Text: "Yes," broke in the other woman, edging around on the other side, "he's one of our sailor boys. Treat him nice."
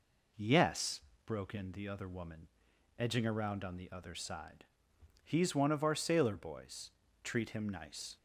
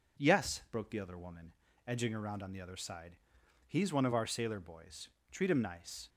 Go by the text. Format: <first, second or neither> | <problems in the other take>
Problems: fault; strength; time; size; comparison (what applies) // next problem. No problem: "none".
first | skips "in"; at 0.8 s